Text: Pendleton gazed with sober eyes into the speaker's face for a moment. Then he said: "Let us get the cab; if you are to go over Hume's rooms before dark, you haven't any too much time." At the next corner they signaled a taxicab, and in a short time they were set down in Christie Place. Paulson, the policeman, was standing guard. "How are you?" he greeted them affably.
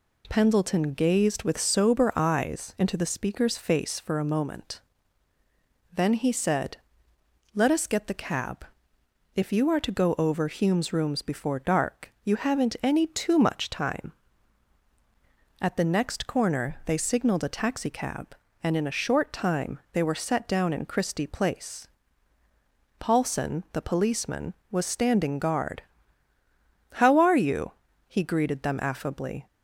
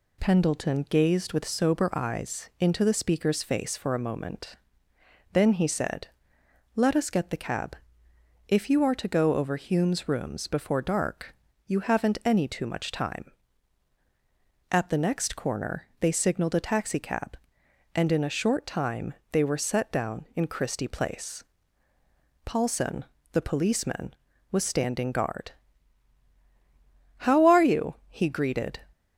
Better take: first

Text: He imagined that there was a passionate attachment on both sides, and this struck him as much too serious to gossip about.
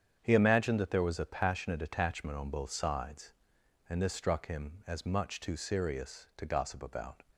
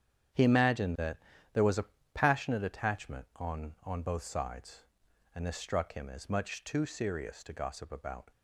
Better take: first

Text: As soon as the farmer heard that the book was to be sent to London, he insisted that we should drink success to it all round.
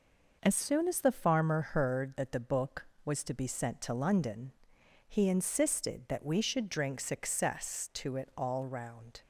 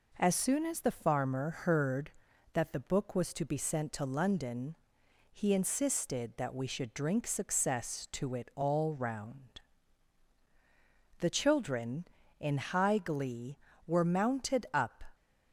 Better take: first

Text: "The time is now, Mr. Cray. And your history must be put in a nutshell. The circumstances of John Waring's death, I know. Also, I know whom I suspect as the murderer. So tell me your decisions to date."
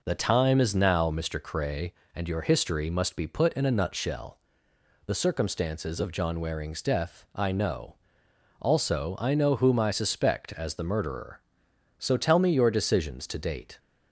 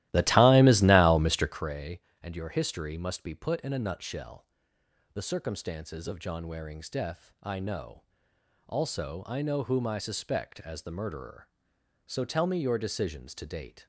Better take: first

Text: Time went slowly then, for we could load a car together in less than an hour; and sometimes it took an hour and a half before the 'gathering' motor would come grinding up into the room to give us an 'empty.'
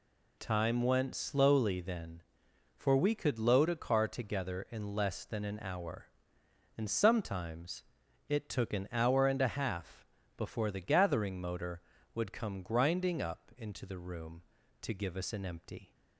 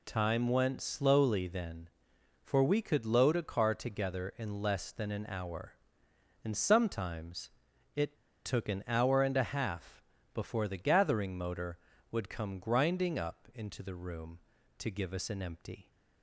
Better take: first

